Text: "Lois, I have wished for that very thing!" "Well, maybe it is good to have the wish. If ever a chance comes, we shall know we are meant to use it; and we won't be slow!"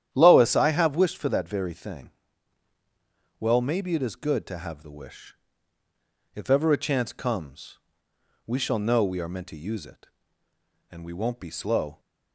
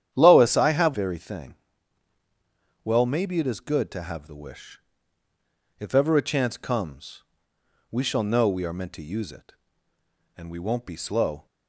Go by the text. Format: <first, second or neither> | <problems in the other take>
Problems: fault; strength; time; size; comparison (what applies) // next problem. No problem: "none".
first | starts louder than the rest; strong; until 1.1 s; 10 dB; strong in the first // skips "wished for that"; at 0.9 s